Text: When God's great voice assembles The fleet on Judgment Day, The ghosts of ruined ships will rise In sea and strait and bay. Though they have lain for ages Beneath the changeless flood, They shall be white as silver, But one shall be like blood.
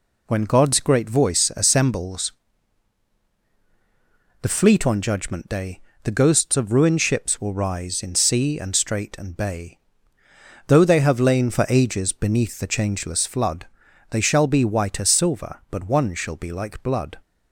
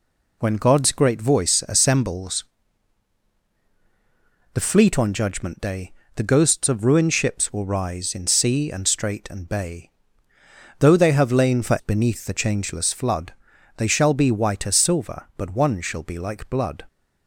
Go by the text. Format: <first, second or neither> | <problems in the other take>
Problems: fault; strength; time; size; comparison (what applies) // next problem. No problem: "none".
first | pauses between "assembles" and "The"; strong; at 2.4 s; 2.1 s long; strong in the first // skips "ages"; at 11.7 s